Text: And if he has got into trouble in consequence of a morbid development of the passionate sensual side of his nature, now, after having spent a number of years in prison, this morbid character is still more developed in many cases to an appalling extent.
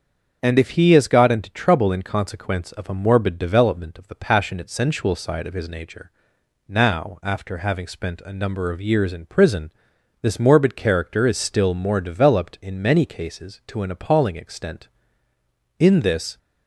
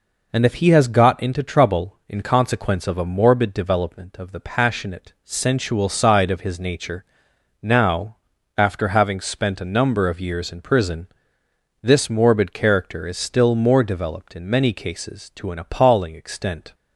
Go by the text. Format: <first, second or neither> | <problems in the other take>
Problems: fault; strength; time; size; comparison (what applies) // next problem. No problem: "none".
second | starts louder than the rest; until 1.4 s; 7 dB // goes on to say "In this"; from 15.7 s on; 0.60 s long